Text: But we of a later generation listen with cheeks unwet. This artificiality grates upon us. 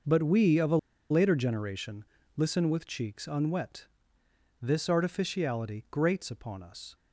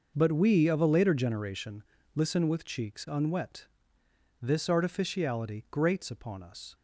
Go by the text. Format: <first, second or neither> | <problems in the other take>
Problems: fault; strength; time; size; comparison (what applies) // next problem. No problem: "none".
second | pauses between "a" and "later"; slight; at 0.7 s; 0.33 s long // pauses between "generation" and "listen"; slight; at 2.0 s; 0.32 s long; slight in the second